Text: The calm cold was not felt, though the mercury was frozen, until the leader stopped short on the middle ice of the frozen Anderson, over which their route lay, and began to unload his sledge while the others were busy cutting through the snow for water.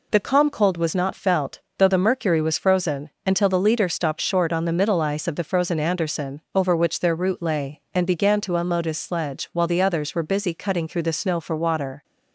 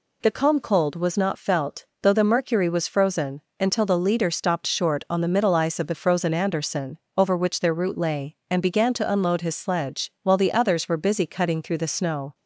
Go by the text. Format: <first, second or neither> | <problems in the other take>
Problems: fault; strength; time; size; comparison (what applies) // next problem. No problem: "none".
first | stops before "for water"; at 12.3 s